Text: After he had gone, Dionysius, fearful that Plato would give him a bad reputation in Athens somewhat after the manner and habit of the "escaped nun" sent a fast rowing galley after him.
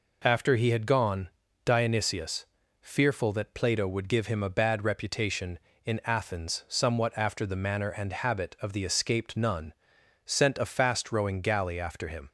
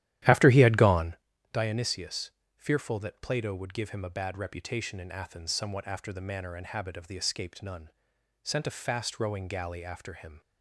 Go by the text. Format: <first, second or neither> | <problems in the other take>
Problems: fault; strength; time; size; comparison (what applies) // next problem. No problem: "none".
first | starts louder than the rest; strong; until 1.2 s; 13 dB // pauses between "nun" and "sent"; noticeable; at 7.8 s; 0.52 s long; noticeable in the first